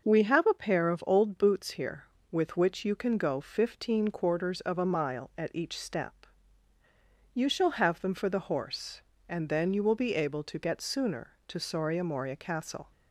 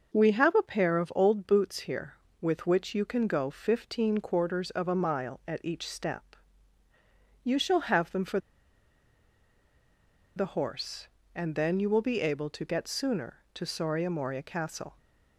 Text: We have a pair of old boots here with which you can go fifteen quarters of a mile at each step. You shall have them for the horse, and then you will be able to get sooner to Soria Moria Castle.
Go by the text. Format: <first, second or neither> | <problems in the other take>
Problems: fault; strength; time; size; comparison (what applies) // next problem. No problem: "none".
first | pauses between "for" and "the"; strong; at 8.3 s; 1.9 s long